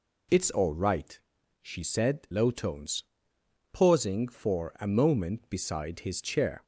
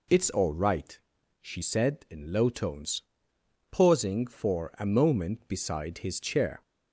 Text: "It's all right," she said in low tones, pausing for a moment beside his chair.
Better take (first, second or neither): second